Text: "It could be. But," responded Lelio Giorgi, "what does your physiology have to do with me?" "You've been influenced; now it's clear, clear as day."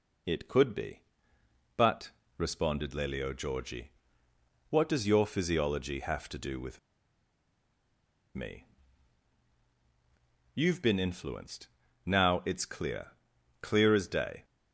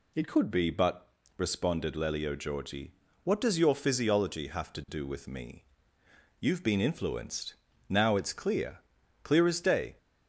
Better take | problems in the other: second | pauses between "with" and "me"; strong; at 6.7 s; 1.5 s long

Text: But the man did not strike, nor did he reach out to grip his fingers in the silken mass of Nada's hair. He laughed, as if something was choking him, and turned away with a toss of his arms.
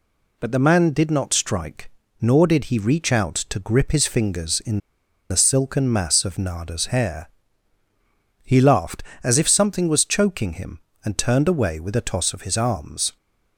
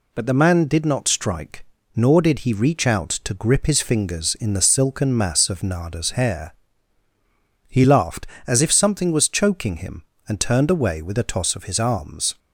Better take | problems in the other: second | pauses between "in" and "the"; noticeable; at 4.7 s; 0.51 s long

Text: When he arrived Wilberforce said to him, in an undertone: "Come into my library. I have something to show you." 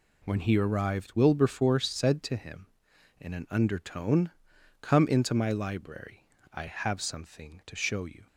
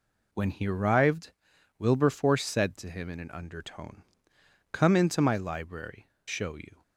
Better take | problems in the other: first | pauses between "arrived" and "Wilberforce"; noticeable; at 1.3 s; 0.48 s long // skips "I have something to"; at 6.1 s

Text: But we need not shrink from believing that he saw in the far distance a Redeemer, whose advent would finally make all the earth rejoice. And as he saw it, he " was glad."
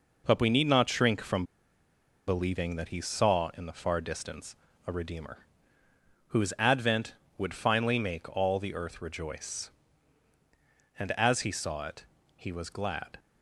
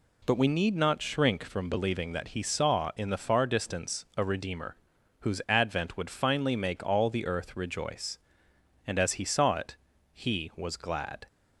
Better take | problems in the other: second | pauses between "from" and "believing"; noticeable; at 1.4 s; 0.84 s long // pauses between "distance" and "a"; slight; at 4.5 s; 0.32 s long

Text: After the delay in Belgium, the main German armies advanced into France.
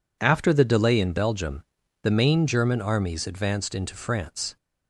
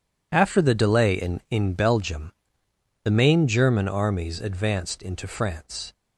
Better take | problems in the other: first | says "in" twice; at 1.5 s

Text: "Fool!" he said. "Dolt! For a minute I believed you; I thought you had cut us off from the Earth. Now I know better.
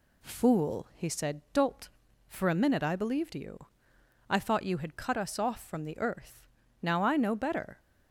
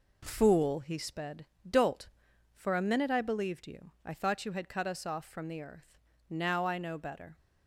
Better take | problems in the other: first | says "sped" for "said"; at 0.9 s

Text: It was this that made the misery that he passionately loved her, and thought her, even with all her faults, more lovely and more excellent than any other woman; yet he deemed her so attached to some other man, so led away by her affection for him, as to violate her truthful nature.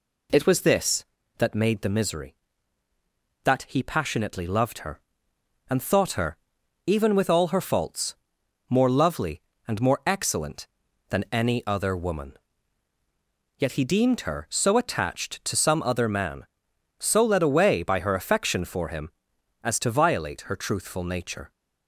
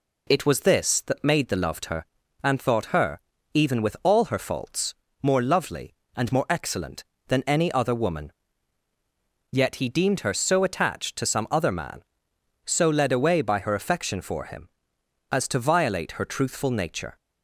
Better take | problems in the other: first | skips "misery that he passionately"; at 1.5 s

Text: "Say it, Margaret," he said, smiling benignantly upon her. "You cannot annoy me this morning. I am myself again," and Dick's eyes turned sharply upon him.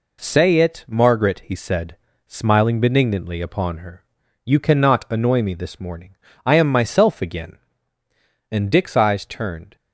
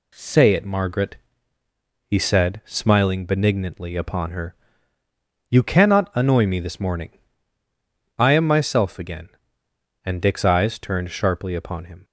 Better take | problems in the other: second | stops before "sharply upon him"; at 9.7 s

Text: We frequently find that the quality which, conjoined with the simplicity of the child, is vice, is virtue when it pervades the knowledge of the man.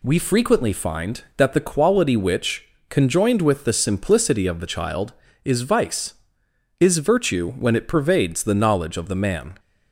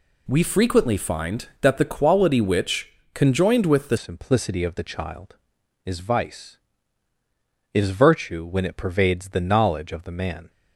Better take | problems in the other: first | changes voice at "simplicity"; from 3.9 s on; 6.5 s long

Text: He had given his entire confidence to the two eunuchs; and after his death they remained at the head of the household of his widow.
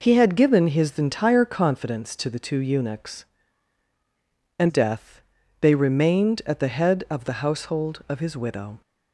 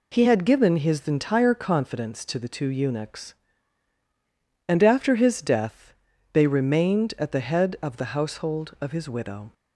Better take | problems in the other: second | skips "after his"; at 4.6 s // pauses between "death" and "they"; at 5.2 s; 0.40 s long; also in the second

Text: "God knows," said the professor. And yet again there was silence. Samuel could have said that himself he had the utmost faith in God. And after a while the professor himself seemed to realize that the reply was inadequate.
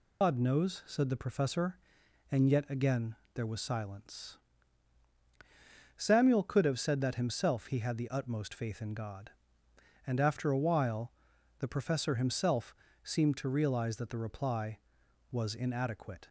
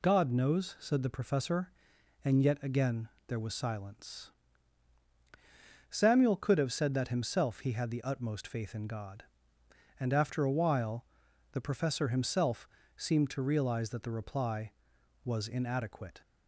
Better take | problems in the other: second | loses the start of "God"; at 0.2 s; 110 ms // pauses between "again" and "there"; slight; at 3.1 s; 0.20 s long; slight in the second // pauses between "while" and "the"; noticeable; at 11.1 s; 0.48 s long; noticeable in the second // pauses between "himself" and "seemed"; slight; at 12.7 s; 0.28 s long; slight in the second

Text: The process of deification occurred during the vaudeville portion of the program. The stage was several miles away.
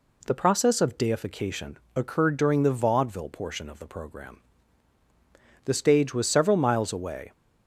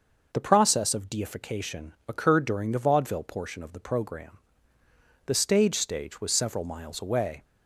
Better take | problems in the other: first | pauses between "deification" and "occurred"; slight; at 1.9 s; 0.16 s long; slight in the first // says "stage" twice; at 5.7 s

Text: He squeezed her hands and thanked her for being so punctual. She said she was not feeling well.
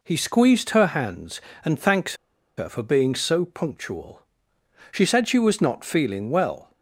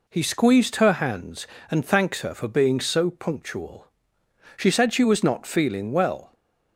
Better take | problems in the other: second | pauses between "thanked" and "her"; at 2.1 s; 0.42 s long

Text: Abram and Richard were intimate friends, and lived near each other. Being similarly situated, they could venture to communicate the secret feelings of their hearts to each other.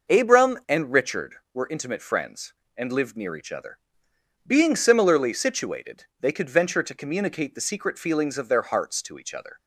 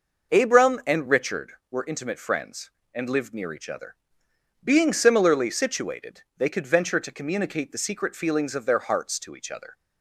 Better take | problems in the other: neither | none

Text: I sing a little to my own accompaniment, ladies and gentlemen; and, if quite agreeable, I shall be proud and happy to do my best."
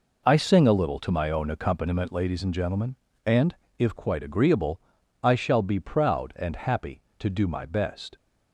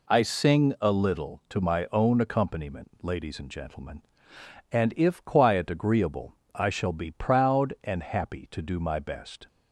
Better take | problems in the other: first | says "quiet" for "quite"; at 5.2 s

